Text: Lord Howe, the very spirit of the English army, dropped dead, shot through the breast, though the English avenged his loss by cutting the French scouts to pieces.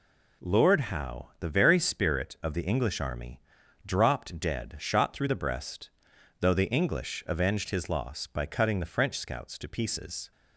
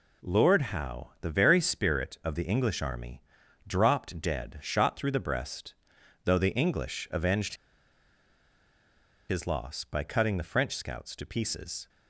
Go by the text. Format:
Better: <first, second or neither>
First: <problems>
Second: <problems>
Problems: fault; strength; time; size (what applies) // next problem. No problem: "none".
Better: first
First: none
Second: pauses between "avenged" and "his"; strong; at 7.5 s; 1.7 s long